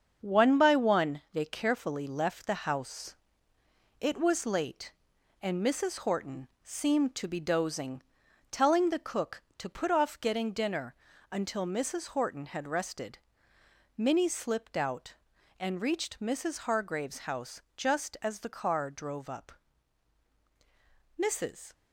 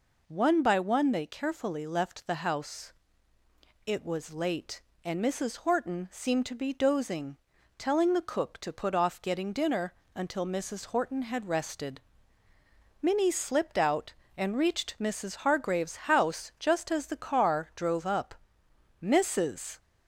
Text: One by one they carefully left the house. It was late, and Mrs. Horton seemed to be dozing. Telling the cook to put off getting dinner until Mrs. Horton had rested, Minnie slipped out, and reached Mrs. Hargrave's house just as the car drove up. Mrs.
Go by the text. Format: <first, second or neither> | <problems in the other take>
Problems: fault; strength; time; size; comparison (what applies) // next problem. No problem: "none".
second | gets quieter; noticeable; throughout; 5.5 dB // pauses between "Horton" and "seemed"; slight; at 6.4 s; 0.16 s long // pauses between "dinner" and "until"; at 10.9 s; 0.38 s long; slight in the second // pauses between "house" and "just"; slight; at 17.6 s; 0.16 s long